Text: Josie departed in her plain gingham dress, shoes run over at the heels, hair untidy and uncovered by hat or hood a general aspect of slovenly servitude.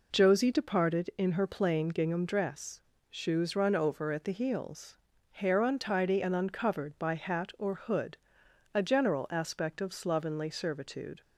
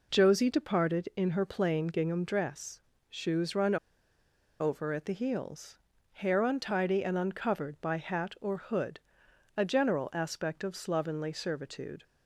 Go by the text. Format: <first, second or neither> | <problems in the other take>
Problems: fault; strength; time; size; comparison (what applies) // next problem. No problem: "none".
first | pauses between "run" and "over"; noticeable; at 3.7 s; 0.84 s long // pauses between "hood" and "a"; noticeable; at 8.9 s; 0.56 s long; noticeable in the first